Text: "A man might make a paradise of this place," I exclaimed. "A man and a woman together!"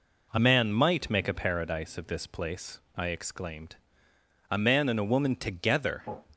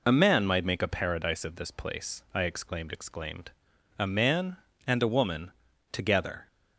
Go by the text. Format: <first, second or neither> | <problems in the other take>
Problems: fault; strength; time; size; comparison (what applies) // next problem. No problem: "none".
first | says "exclaimed" twice; at 2.9 s // pauses between "woman" and "together"; at 5.5 s; 0.40 s long